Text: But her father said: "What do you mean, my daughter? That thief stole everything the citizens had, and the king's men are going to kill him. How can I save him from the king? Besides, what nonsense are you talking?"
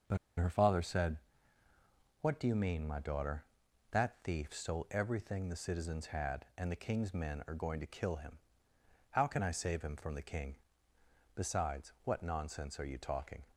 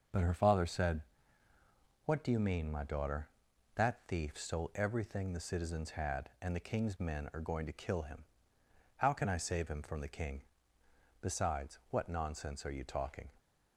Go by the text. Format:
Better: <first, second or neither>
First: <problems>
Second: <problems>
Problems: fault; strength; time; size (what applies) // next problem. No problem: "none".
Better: second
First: starts louder than the rest; until 2.3 s; 6.5 dB // pauses between "But" and "her"; slight; at 0.1 s; 0.21 s long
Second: starts louder than the rest; until 2.1 s; 6.5 dB